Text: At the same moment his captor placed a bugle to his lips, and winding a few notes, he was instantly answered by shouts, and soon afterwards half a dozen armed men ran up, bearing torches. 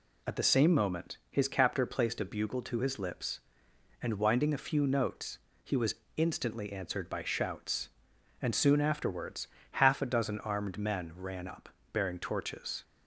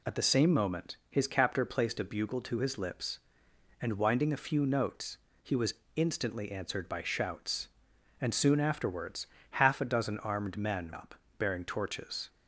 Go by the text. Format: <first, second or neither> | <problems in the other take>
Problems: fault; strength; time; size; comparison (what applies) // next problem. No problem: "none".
first | pauses between "was" and "instantly"; slight; at 5.7 s; 0.20 s long; slight in the first // pauses between "afterwards" and "half"; slight; at 9.2 s; 0.26 s long; slight in the first // skips "ran"; at 10.9 s